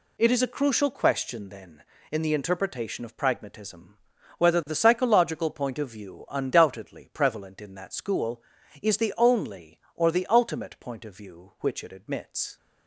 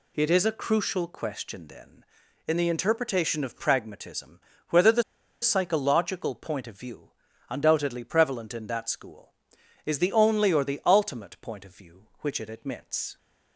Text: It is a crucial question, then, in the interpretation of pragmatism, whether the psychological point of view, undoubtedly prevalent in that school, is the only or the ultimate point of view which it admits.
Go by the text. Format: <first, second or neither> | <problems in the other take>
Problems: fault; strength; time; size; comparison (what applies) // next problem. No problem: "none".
first | pauses between "the" and "psychological"; at 5.0 s; 0.39 s long